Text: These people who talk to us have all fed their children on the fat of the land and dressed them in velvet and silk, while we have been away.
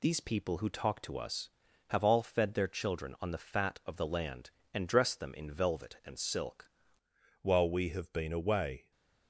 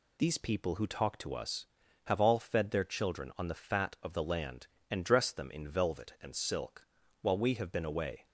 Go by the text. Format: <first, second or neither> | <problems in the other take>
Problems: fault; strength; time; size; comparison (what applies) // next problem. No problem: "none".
second | changes voice at "while"; from 7.4 s on; 1.5 s long